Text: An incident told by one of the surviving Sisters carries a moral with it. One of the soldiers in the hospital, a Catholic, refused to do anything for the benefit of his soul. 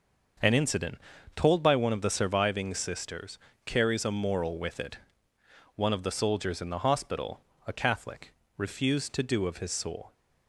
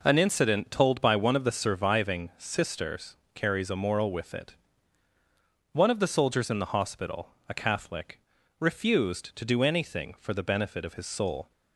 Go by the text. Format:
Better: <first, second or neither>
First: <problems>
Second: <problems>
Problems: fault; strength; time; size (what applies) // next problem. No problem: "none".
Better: second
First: starts louder than the rest; until 1.7 s; 6.5 dB // pauses between "incident" and "told"; slight; at 0.9 s; 0.36 s long // pauses between "Sisters" and "carries"; slight; at 3.3 s; 0.26 s long // skips "anything for the benefit"; at 9.4 s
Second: pauses between "Sisters" and "carries"; slight; at 3.1 s; 0.20 s long